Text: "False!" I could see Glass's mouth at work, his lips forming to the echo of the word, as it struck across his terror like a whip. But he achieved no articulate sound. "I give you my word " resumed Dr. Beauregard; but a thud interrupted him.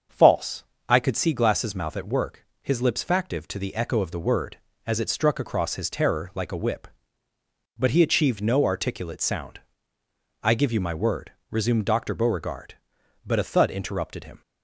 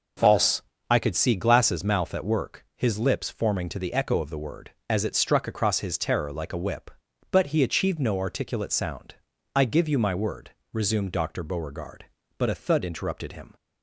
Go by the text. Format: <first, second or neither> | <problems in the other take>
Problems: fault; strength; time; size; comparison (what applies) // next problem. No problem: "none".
second | starts louder than the rest; until 1.3 s; 6.5 dB // says "factive" for "forming"; at 3.0 s